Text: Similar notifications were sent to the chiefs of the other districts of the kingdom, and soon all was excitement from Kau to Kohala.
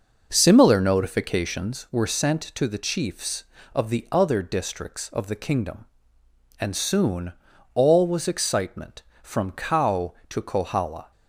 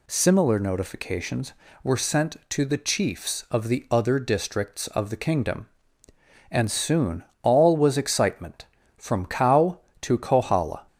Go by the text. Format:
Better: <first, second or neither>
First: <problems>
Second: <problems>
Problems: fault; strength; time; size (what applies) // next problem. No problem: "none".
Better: second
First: starts louder than the rest; noticeable; until 1.9 s; 6 dB // pauses between "soon" and "all"; at 7.3 s; 0.42 s long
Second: pauses between "soon" and "all"; slight; at 7.2 s; 0.18 s long